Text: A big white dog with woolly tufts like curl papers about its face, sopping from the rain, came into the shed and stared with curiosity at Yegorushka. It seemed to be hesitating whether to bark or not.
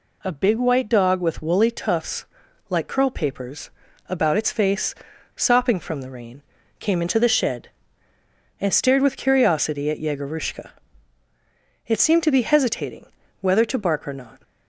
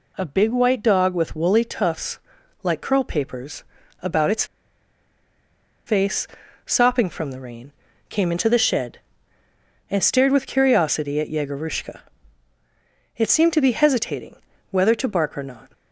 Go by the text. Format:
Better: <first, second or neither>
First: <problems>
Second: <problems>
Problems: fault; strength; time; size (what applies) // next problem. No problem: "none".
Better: first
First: pauses between "tufts" and "like"; at 2.2 s; 0.44 s long // pauses between "papers" and "about"; at 3.7 s; 0.38 s long // pauses between "hesitating" and "whether"; slight; at 13.0 s; 0.34 s long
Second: pauses between "tufts" and "like"; at 2.1 s; 0.44 s long // pauses between "papers" and "about"; at 3.6 s; 0.38 s long // pauses between "its" and "face"; strong; at 4.4 s; 1.4 s long // pauses between "hesitating" and "whether"; slight; at 14.3 s; 0.34 s long